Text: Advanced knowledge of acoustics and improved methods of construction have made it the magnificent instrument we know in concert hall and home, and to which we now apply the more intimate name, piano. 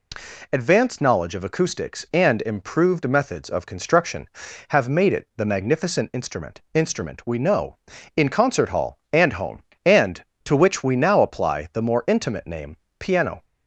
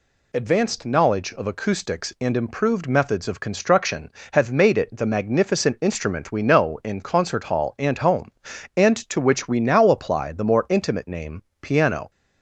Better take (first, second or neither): second